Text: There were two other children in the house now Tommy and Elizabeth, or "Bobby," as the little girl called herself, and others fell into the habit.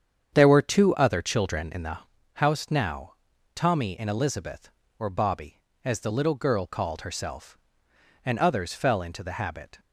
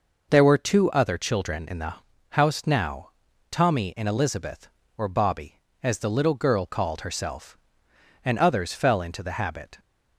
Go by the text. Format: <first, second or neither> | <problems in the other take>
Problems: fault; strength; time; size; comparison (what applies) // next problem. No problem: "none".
second | starts louder than the rest; strong; until 2.0 s; 8 dB // pauses between "the" and "house"; slight; at 1.9 s; 0.36 s long; slight in the second // pauses between "now" and "Tommy"; at 3.1 s; 0.40 s long; also in the second